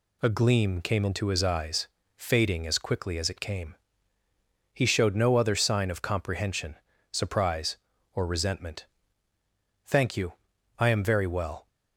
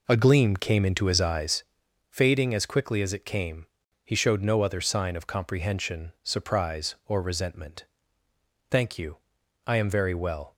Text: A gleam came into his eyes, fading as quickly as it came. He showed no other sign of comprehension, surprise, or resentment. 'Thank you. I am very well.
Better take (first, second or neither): first